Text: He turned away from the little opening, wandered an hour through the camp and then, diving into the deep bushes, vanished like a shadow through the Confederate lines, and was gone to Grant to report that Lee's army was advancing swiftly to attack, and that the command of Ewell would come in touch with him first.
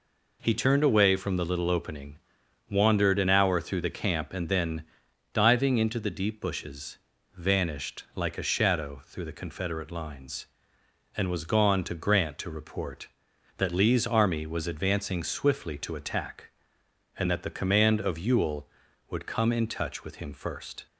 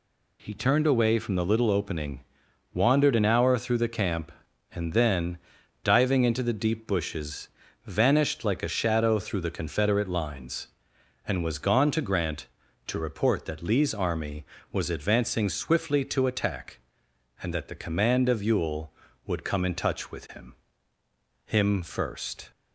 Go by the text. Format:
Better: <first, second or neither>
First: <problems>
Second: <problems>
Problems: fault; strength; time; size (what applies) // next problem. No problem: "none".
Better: first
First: none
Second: says "him" twice; at 21.4 s